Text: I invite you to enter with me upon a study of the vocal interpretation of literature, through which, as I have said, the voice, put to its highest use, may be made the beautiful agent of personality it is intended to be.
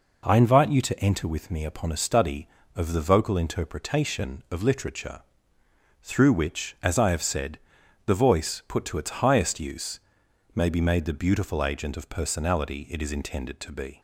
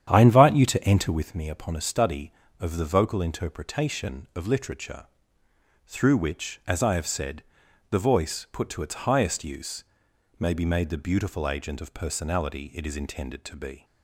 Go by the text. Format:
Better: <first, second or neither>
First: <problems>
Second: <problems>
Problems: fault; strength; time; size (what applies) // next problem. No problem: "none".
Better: first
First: none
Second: starts louder than the rest; strong; until 1.4 s; 9.5 dB